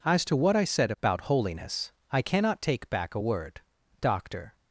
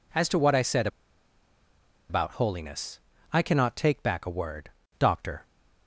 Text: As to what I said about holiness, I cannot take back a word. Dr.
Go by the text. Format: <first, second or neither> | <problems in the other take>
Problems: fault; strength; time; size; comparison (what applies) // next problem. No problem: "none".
first | pauses between "said" and "about"; at 0.8 s; 1.2 s long